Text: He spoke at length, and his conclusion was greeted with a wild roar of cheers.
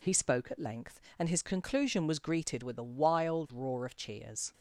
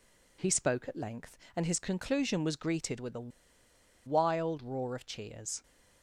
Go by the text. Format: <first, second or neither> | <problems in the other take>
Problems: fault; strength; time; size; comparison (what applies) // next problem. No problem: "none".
first | pauses between "a" and "wild"; noticeable; at 3.2 s; 0.76 s long